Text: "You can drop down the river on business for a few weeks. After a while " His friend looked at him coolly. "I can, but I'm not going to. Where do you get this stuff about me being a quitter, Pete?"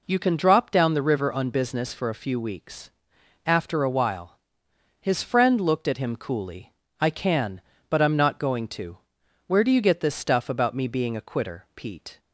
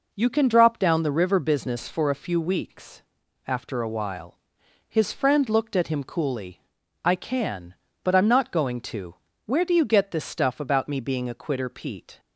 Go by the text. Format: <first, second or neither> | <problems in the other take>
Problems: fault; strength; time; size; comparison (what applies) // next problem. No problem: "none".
first | skips "on"; at 1.3 s